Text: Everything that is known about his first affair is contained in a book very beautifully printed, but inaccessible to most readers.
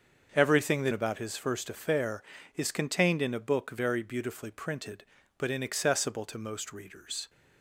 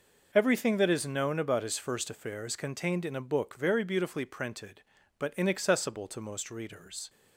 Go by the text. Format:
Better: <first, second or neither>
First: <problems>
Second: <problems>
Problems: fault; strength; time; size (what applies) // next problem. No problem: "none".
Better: second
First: starts louder than the rest; until 1.3 s; 6.5 dB // skips "is known"; at 0.9 s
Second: none